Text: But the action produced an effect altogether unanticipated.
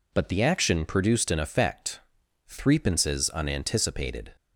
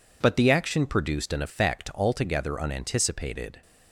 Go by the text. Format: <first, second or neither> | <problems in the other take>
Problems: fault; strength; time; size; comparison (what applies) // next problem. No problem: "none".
second | says "threepences" for "altogether"; at 2.4 s